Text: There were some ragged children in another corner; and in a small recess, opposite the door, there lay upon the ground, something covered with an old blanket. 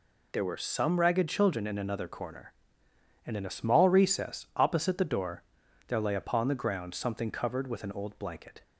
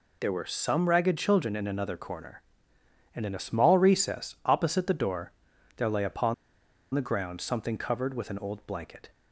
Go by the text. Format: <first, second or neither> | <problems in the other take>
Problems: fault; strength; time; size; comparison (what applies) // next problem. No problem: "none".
first | pauses between "upon" and "the"; noticeable; at 6.3 s; 0.60 s long